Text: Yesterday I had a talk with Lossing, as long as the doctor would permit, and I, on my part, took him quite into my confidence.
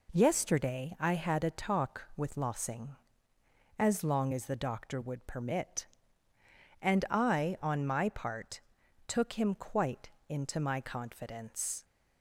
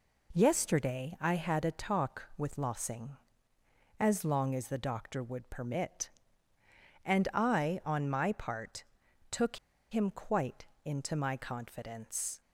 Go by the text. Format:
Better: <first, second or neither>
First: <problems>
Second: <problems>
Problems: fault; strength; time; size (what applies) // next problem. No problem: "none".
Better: first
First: pauses between "quite" and "into"; slight; at 10.0 s; 0.22 s long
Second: pauses between "took" and "him"; slight; at 9.5 s; 0.33 s long // pauses between "quite" and "into"; slight; at 10.6 s; 0.22 s long